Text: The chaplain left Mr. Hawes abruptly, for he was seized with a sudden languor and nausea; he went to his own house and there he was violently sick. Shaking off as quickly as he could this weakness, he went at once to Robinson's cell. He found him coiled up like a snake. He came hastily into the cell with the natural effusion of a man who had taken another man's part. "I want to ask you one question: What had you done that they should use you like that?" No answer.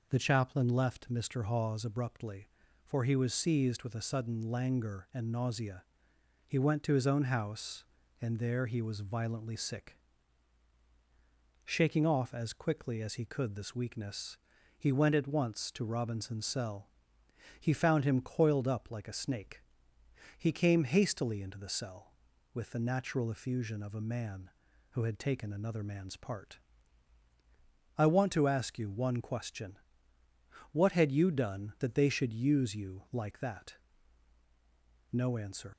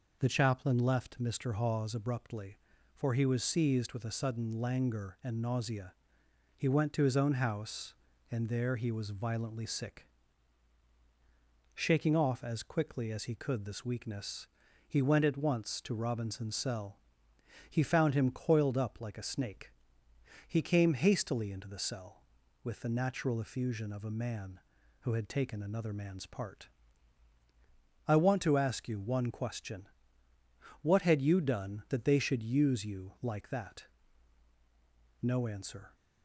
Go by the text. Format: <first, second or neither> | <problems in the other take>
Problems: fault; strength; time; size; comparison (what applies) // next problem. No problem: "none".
second | leaves "answer" unfinished; at 35.7 s; 115 ms